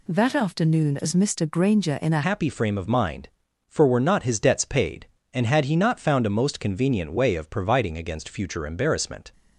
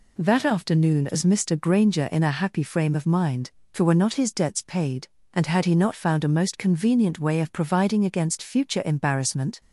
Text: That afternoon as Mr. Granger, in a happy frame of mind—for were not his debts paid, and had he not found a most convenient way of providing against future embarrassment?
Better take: second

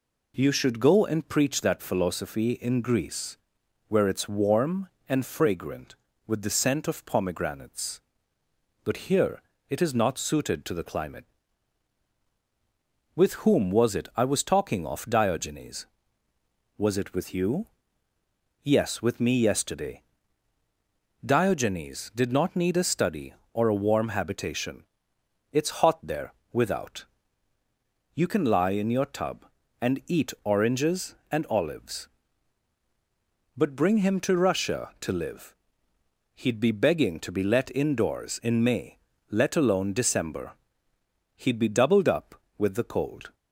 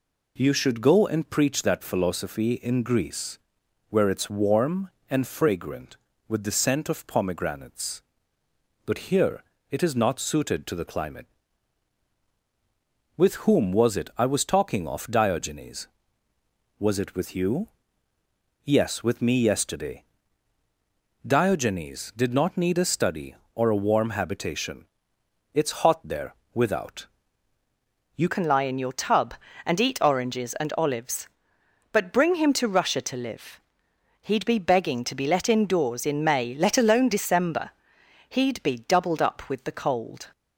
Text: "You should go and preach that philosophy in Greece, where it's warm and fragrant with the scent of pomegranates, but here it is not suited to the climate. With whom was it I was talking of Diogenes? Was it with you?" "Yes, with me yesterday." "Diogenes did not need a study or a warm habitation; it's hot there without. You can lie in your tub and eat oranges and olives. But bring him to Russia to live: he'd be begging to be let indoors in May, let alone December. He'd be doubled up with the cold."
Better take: first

